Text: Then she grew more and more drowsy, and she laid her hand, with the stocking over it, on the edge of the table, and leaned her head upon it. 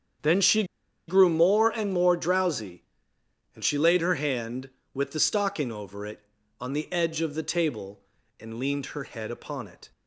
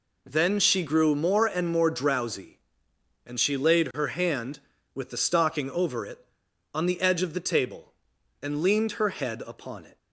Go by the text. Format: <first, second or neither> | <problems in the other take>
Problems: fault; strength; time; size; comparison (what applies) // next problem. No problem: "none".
second | starts louder than the rest; strong; until 1.6 s; 8.5 dB // pauses between "she" and "grew"; at 0.6 s; 0.44 s long